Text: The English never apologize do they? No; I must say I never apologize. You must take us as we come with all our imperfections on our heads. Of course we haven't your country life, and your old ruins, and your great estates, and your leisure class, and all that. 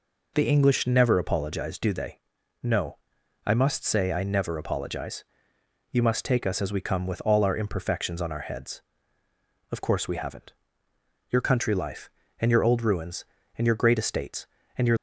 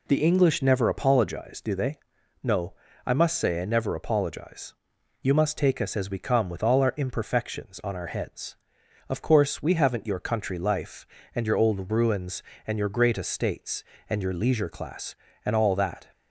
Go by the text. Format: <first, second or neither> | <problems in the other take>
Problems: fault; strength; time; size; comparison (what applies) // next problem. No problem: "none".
second | pauses between "haven't" and "your"; noticeable; at 10.5 s; 0.76 s long // stops before "leisure class and all that"; at 14.9 s